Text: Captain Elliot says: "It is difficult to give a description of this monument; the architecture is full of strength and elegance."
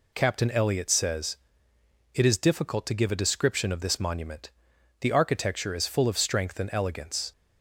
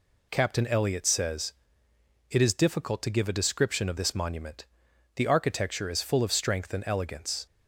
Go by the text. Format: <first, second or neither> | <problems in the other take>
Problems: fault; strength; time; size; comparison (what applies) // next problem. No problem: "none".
neither | none